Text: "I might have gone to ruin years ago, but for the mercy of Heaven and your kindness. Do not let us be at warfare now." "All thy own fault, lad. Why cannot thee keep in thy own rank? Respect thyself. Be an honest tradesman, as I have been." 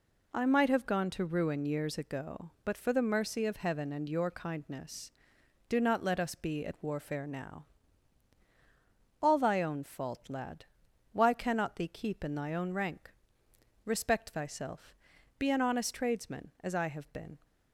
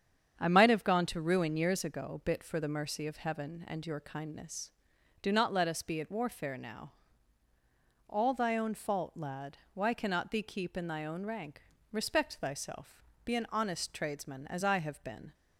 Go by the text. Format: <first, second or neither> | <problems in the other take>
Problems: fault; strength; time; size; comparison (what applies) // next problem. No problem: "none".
first | starts louder than the rest; strong; until 1.4 s; 8 dB // says "bit" for "but"; at 2.2 s